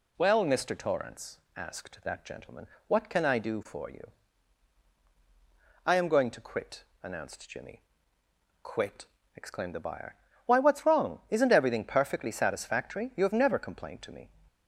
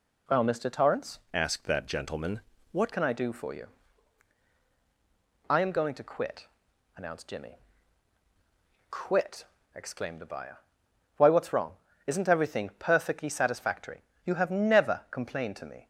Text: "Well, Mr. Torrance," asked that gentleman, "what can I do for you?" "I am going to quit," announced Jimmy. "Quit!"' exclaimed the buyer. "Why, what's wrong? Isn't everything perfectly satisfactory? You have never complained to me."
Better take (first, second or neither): first